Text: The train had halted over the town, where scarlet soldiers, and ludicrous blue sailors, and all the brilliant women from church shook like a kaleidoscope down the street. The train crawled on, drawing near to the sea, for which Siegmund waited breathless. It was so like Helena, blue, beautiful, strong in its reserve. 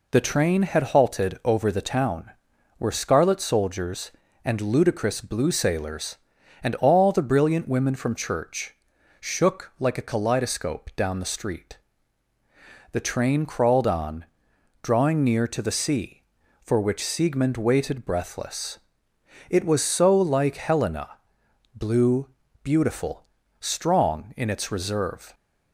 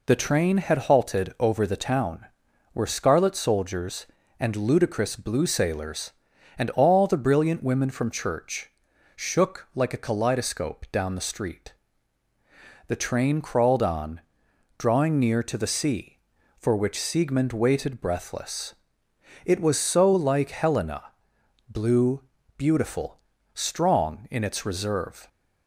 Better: neither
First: pauses between "church" and "shook"; noticeable; at 8.7 s; 0.46 s long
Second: pauses between "church" and "shook"; noticeable; at 8.6 s; 0.46 s long

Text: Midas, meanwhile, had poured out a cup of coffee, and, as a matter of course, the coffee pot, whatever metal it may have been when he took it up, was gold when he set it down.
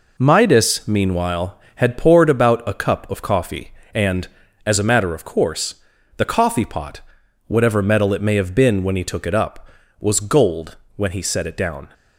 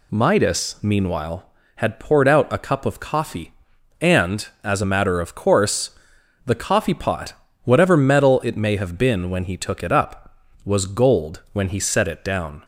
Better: second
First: says "about" for "out"; at 2.3 s // pauses between "gold" and "when"; slight; at 10.7 s; 0.20 s long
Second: none

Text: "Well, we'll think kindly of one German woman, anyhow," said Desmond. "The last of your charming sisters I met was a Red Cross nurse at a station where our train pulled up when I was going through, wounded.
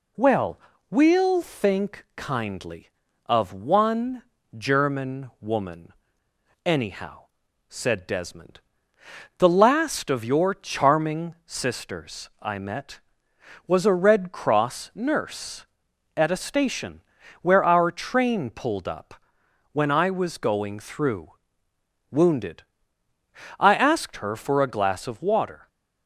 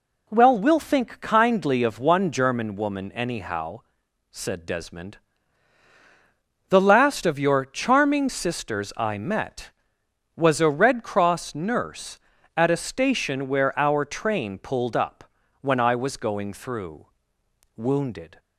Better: second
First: pauses between "one" and "German"; slight; at 4.2 s; 0.34 s long // pauses between "station" and "where"; at 17.0 s; 0.40 s long // pauses between "up" and "when"; noticeable; at 19.1 s; 0.56 s long // goes on to say "I asked her for a glass of water"; strong; from 23.5 s on; 2.0 s long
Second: pauses between "up" and "when"; slight; at 15.2 s; 0.36 s long

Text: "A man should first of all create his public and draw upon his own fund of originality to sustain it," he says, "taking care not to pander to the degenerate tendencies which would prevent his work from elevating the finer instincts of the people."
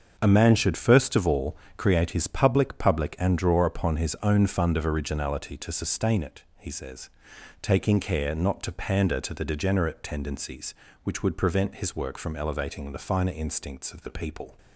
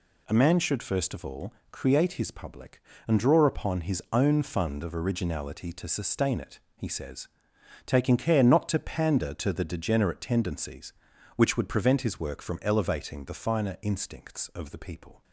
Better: second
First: starts louder than the rest; until 1.2 s; 7 dB // pauses between "all" and "create"; slight; at 1.5 s; 0.22 s long // says "public" twice; at 2.7 s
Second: pauses between "all" and "create"; slight; at 1.5 s; 0.18 s long

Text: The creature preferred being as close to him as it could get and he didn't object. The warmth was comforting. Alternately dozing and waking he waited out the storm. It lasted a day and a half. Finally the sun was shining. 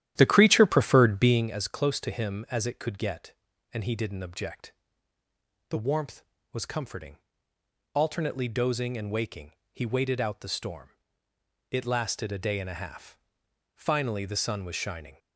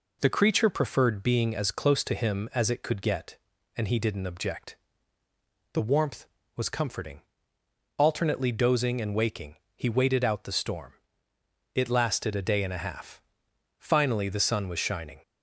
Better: second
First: starts louder than the rest; strong; until 1.5 s; 12 dB // pauses between "waking" and "he"; slight; at 9.5 s; 0.20 s long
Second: pauses between "waking" and "he"; slight; at 9.5 s; 0.20 s long

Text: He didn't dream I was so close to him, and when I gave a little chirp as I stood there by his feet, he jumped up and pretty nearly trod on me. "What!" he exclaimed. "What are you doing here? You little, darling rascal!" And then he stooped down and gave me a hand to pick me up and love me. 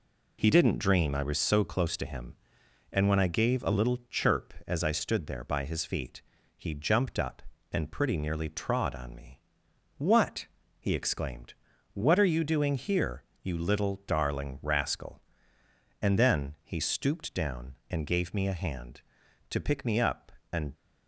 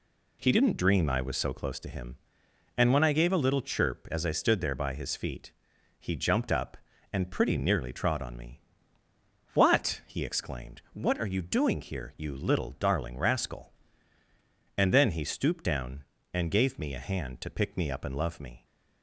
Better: second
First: stops before "love me"; at 20.7 s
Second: none

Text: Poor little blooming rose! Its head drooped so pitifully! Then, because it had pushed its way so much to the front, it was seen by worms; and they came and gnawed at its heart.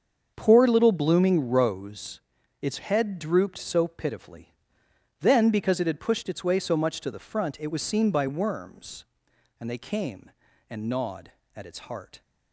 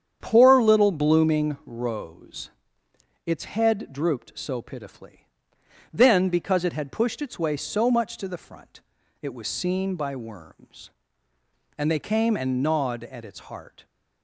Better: neither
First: starts louder than the rest; until 1.3 s; 7 dB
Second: starts louder than the rest; strong; until 1.2 s; 8.5 dB

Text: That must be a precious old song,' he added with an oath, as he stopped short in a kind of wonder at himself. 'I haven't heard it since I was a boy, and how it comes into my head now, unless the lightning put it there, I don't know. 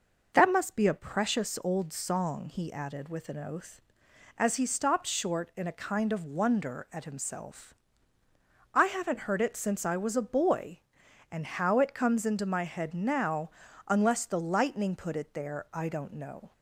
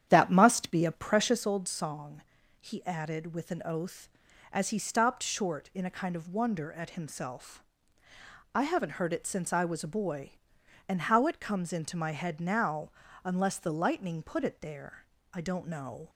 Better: first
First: none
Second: starts louder than the rest; strong; until 1.5 s; 9.5 dB

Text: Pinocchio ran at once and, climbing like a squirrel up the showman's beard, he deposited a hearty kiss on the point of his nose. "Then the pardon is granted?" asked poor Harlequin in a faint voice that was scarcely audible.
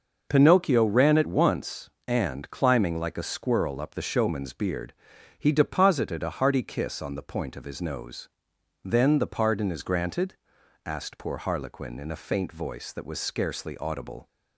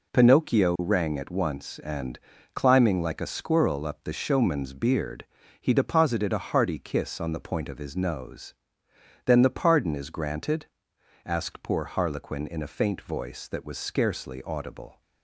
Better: first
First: none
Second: says "rang" for "ran"; at 0.7 s

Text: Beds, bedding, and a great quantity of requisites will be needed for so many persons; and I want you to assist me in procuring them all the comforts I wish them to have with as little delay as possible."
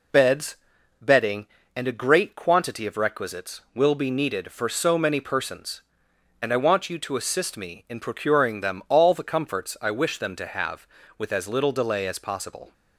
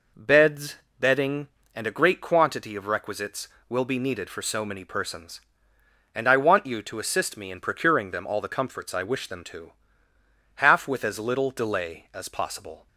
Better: first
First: none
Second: says "half" for "have"; at 10.5 s

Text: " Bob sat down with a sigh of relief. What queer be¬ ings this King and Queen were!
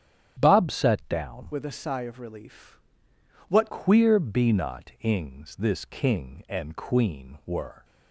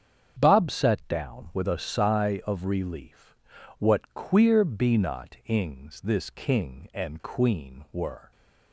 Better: second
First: starts louder than the rest; strong; until 1.4 s; 10 dB // changes voice from "with" to "What"; from 1.5 to 3.7 s; 2.2 s long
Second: starts louder than the rest; strong; until 1.4 s; 8 dB

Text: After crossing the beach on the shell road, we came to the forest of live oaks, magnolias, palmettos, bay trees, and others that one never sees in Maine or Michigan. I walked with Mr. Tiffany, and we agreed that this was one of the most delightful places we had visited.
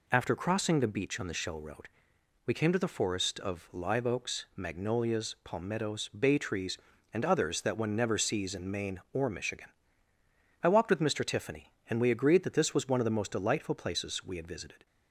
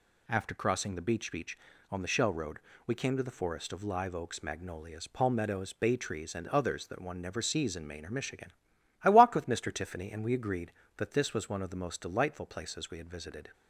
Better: first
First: none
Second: says "beach" twice; at 1.3 s

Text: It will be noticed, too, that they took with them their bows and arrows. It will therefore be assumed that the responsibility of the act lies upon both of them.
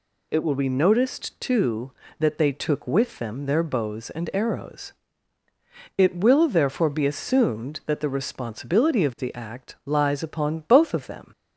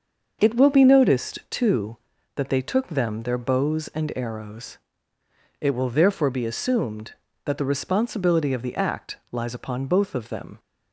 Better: first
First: none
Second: starts louder than the rest; until 1.4 s; 6.5 dB // skips "with"; at 2.8 s // pauses between "act" and "lies"; slight; at 9.1 s; 0.16 s long

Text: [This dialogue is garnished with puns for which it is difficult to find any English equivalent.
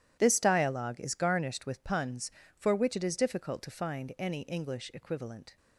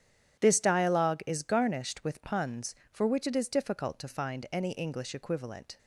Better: neither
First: starts louder than the rest; strong; until 1.2 s; 11.5 dB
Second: starts louder than the rest; strong; until 1.4 s; 10 dB

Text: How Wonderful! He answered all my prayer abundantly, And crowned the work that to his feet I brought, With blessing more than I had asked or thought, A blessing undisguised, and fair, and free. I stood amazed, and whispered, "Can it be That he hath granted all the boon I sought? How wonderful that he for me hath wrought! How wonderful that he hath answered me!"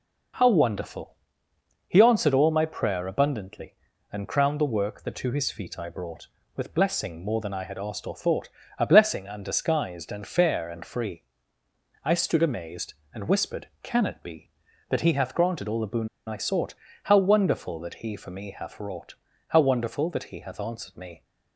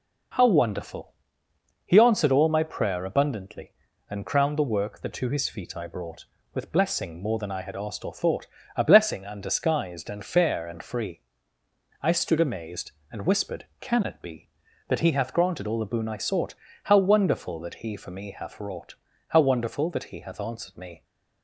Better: second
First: pauses between "boon" and "I"; slight; at 16.0 s; 0.19 s long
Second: none

